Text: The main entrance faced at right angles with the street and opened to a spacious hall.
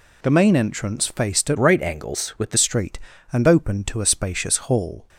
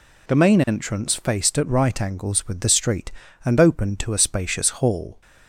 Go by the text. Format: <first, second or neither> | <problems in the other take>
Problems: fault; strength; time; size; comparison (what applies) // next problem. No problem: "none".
second | changes voice from "right" to "the"; from 1.5 to 2.5 s; 1.0 s long